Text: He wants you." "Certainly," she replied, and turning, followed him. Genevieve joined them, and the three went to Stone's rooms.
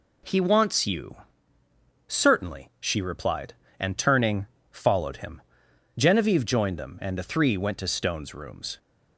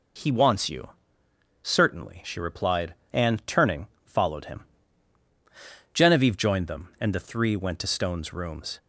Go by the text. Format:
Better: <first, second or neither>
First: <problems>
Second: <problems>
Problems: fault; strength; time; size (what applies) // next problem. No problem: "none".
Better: neither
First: none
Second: none